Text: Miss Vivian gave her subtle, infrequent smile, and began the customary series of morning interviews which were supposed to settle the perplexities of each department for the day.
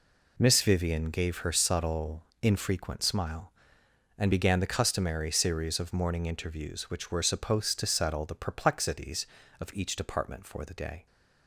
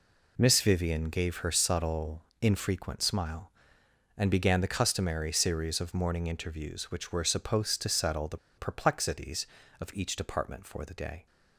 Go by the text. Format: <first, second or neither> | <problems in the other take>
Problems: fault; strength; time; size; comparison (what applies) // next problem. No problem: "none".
first | pauses between "the" and "perplexities"; slight; at 8.3 s; 0.20 s long